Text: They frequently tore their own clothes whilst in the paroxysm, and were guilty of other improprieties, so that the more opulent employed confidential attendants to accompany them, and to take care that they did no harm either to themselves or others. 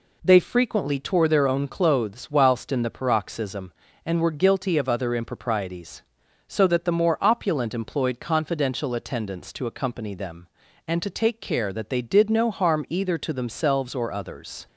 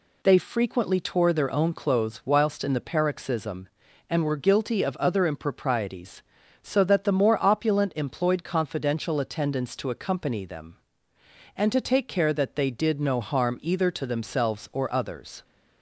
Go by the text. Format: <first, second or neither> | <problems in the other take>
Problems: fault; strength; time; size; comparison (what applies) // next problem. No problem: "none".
neither | none